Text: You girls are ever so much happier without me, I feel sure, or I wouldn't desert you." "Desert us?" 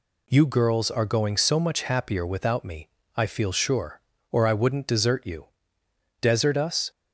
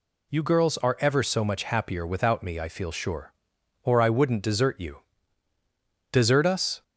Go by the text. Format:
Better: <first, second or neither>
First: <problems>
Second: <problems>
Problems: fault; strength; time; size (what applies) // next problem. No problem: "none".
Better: second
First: says "going" for "ever"; at 1.0 s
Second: none